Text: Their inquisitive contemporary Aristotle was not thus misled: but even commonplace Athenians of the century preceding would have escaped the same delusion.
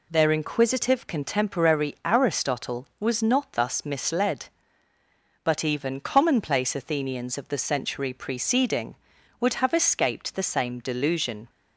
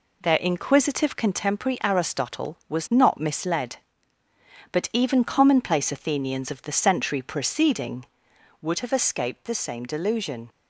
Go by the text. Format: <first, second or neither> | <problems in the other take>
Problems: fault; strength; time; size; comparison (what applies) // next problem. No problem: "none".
first | skips "thus"; at 3.2 s